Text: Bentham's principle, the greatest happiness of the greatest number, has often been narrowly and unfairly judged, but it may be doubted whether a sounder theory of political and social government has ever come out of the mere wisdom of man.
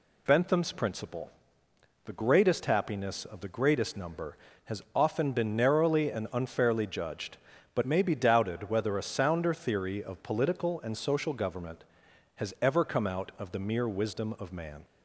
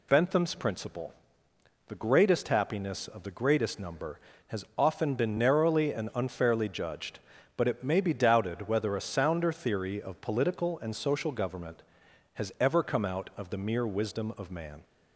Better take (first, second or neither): second